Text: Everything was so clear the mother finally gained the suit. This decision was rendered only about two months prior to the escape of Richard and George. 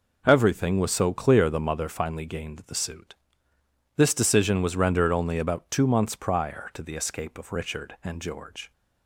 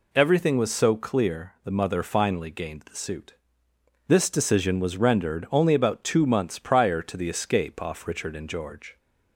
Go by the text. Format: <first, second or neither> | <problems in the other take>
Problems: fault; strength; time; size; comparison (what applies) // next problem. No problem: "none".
first | says "off" for "of"; at 7.8 s